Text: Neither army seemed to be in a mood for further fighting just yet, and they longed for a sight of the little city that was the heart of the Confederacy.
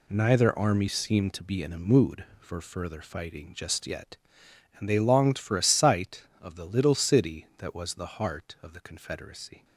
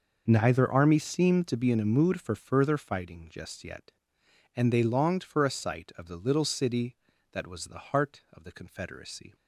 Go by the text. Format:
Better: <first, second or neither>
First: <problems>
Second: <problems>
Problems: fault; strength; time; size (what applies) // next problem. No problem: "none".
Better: neither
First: none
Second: none